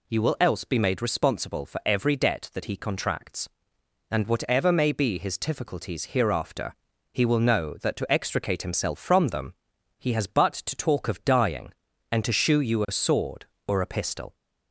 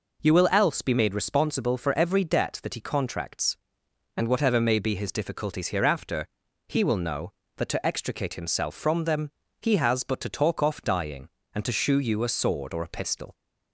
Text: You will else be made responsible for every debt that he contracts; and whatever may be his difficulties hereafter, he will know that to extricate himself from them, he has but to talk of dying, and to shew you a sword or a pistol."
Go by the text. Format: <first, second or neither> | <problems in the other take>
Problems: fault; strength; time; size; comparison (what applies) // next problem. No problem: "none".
first | says "off" for "of"; at 10.6 s